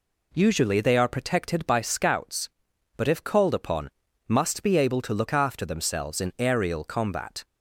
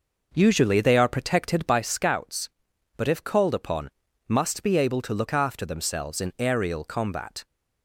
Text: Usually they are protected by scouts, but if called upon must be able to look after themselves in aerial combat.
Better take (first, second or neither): first